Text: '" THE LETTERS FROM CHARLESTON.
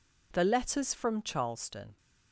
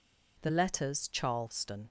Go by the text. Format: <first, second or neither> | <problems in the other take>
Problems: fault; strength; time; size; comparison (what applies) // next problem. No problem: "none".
first | skips "FROM"; at 1.0 s